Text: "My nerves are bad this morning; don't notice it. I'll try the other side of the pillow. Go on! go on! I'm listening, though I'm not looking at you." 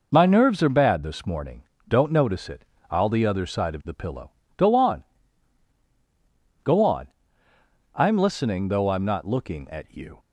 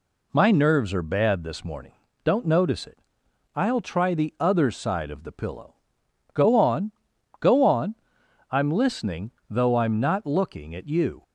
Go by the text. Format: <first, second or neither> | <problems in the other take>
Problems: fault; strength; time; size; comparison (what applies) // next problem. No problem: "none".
second | skips "try"; at 3.0 s